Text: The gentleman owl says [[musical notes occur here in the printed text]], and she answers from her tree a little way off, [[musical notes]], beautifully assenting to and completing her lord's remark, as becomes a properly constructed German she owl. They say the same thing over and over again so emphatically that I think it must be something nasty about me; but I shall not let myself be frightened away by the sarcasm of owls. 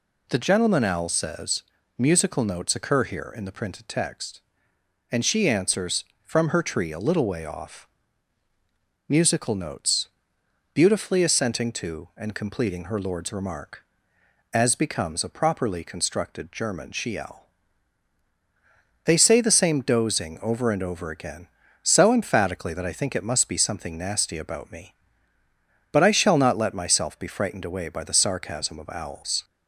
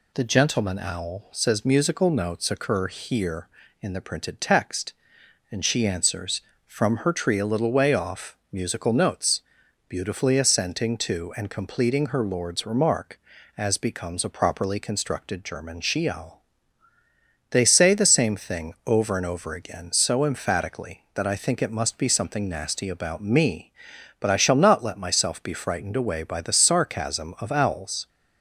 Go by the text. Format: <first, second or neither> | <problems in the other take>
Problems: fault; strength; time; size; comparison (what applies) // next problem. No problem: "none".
second | pauses between "says" and "musical"; slight; at 1.6 s; 0.36 s long // says "dozing" for "thing"; at 19.8 s